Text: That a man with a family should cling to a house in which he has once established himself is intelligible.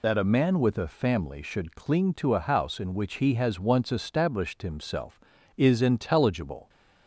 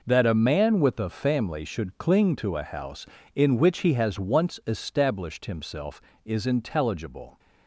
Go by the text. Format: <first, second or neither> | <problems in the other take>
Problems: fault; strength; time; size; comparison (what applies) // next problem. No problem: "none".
second | loses the start of "That"; at 0.0 s; 50 ms